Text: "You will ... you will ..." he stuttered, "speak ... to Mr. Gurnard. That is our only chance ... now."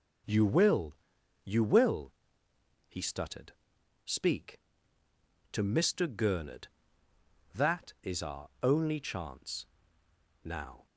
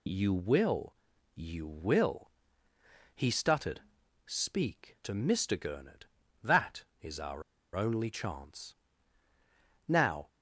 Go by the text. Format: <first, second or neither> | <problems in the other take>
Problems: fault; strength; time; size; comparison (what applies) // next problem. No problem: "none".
first | pauses between "our" and "only"; slight; at 7.4 s; 0.33 s long